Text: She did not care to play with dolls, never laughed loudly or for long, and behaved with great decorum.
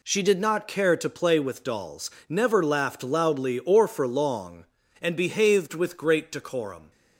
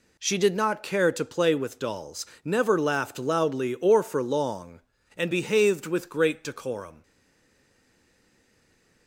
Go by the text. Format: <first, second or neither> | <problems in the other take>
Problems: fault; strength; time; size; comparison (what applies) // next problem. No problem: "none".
first | stays silent after the last word; noticeable; from 7.0 s on; 2.0 s long